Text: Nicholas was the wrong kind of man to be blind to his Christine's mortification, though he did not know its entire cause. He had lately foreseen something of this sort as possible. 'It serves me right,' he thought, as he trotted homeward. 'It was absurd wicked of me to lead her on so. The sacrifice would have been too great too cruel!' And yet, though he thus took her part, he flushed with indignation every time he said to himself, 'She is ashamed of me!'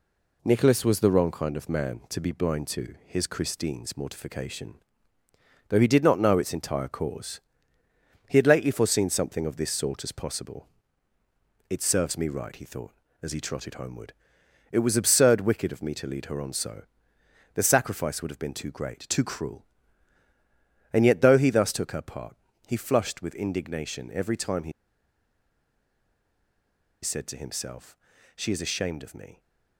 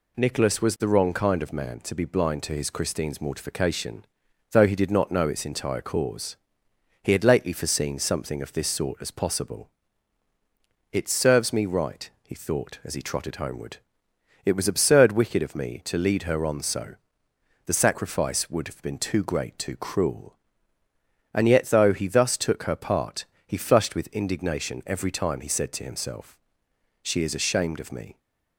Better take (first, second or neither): second